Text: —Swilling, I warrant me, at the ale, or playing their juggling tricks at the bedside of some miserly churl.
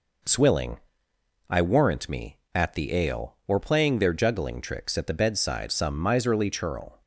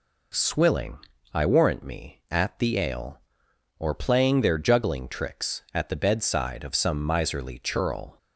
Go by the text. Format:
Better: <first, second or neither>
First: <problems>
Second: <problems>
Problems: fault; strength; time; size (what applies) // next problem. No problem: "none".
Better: second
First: skips "of"; at 5.7 s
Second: none